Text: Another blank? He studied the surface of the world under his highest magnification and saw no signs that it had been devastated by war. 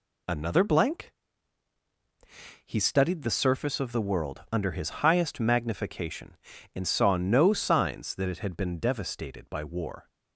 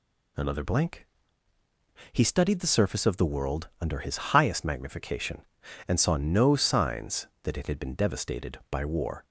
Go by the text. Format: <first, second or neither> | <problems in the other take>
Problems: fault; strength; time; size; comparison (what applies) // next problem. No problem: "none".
second | gets quieter; throughout; 6 dB